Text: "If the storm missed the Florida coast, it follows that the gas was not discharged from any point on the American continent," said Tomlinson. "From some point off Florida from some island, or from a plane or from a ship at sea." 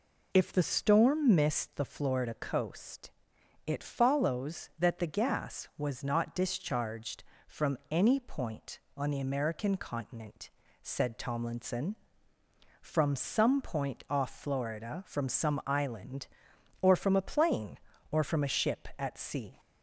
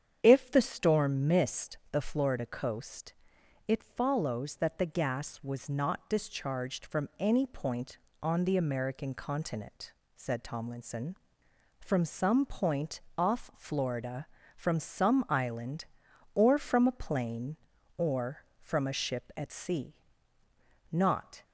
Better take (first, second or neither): first